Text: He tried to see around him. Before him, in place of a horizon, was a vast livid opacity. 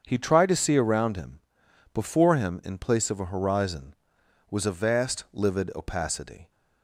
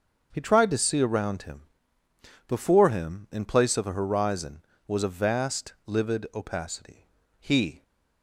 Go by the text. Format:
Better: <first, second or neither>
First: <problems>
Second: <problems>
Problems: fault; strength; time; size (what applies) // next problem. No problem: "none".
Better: first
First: starts louder than the rest; until 1.0 s; 7 dB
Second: starts louder than the rest; until 1.3 s; 6.5 dB // goes on to say "He"; slight; from 7.3 s on; 0.44 s long